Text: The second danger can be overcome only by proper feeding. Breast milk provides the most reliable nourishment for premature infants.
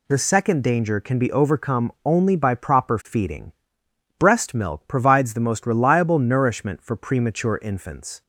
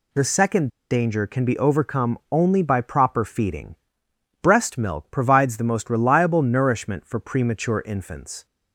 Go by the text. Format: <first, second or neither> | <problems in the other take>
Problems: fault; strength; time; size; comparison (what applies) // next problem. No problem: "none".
first | pauses between "second" and "danger"; slight; at 0.6 s; 0.21 s long